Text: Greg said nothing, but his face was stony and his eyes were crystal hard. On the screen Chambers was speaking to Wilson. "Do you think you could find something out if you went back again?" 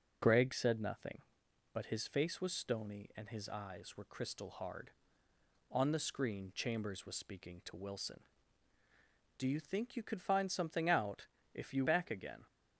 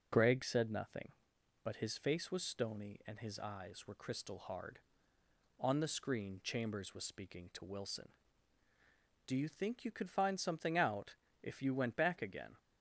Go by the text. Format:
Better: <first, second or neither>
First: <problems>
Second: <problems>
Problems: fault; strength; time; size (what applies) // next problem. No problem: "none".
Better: second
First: starts louder than the rest; until 1.7 s; 6.5 dB // pauses between "out" and "if"; slight; at 11.2 s; 0.26 s long // skips "went"; at 11.8 s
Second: pauses between "out" and "if"; slight; at 11.1 s; 0.26 s long